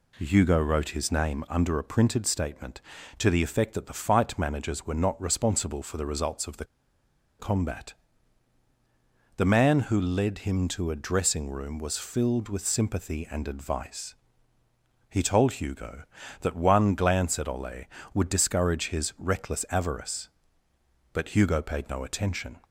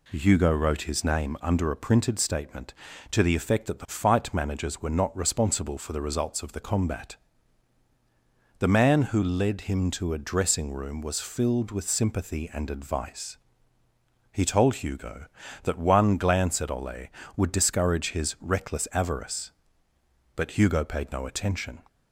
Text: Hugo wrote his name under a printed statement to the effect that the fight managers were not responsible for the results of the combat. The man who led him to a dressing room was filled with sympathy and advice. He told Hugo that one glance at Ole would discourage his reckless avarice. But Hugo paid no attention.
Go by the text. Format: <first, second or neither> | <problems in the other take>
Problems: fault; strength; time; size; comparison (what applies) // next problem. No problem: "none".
second | pauses between "the" and "combat"; noticeable; at 6.6 s; 0.74 s long